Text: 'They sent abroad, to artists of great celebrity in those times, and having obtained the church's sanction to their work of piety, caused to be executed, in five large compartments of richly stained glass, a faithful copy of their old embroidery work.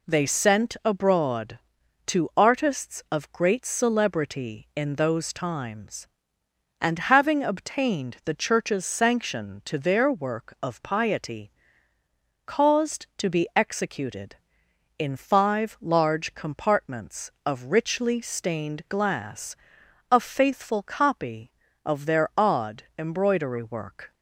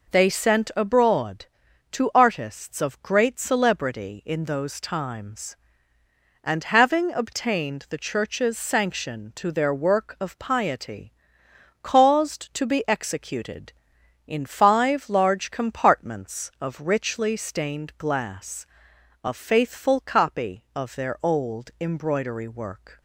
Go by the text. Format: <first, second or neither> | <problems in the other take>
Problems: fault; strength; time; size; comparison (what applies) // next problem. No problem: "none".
second | says "odd" for "old"; at 22.3 s